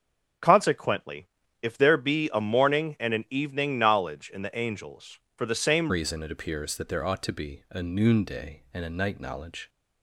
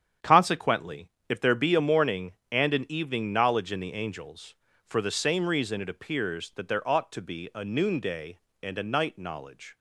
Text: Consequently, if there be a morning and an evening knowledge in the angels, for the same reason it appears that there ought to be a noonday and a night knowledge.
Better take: second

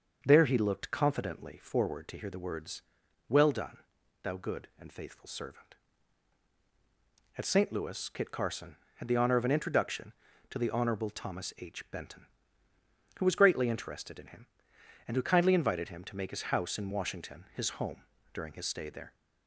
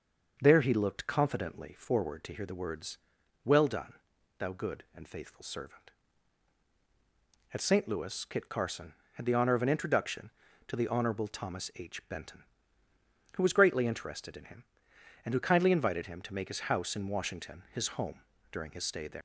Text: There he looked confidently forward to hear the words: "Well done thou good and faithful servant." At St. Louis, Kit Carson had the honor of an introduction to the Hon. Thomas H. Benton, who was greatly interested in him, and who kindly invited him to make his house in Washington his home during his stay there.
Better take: first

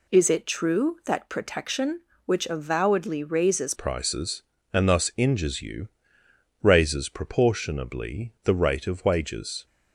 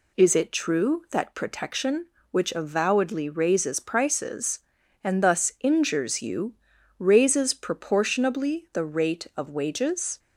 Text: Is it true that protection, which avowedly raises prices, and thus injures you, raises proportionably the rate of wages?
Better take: second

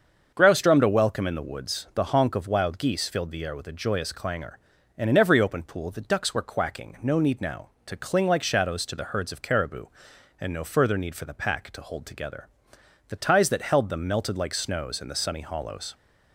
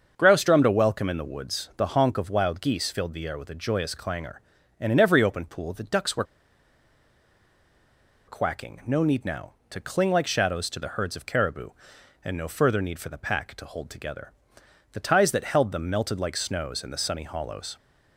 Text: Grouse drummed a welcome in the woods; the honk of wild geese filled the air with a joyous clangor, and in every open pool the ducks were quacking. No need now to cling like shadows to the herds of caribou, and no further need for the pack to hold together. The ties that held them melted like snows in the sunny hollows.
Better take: first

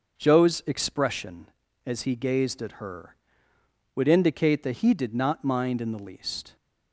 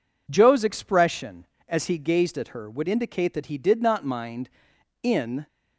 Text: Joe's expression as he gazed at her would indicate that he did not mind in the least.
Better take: first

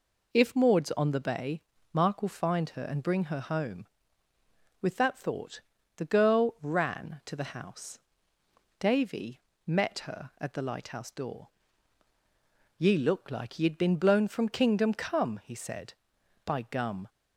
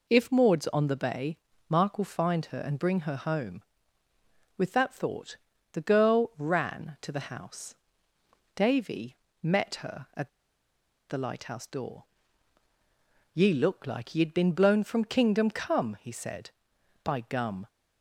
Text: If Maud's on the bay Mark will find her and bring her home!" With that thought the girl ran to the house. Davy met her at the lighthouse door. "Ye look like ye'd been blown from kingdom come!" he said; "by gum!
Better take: first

